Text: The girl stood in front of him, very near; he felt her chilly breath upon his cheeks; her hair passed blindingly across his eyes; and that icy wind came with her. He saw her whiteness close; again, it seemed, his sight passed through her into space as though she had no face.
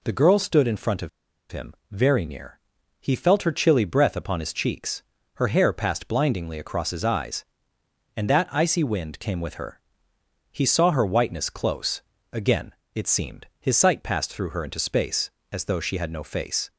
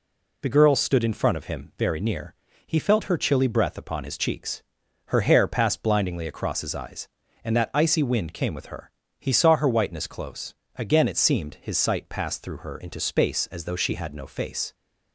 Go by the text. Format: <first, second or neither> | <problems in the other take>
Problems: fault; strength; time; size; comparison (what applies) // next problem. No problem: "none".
second | pauses between "of" and "him"; at 1.0 s; 0.41 s long